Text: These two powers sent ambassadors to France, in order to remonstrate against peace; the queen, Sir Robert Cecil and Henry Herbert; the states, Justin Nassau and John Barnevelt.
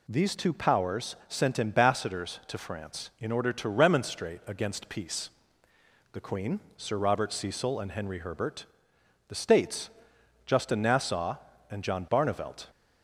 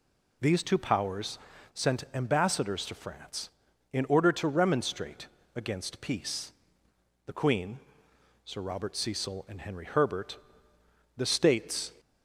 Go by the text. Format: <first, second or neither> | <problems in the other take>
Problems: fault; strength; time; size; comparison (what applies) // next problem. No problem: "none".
first | pauses between "powers" and "sent"; at 1.3 s; 0.36 s long // pauses between "remonstrate" and "against"; slight; at 5.2 s; 0.28 s long // stops before "Justin Nassau and John Barnevelt"; at 11.9 s